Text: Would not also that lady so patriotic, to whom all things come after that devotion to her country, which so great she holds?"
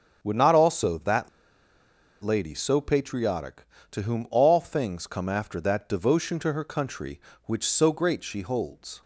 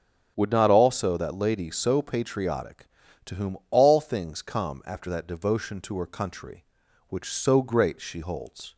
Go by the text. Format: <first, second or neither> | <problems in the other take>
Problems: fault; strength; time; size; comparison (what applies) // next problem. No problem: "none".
second | starts louder than the rest; until 1.2 s; 7 dB; strong in the second // pauses between "that" and "lady"; noticeable; at 1.2 s; 0.94 s long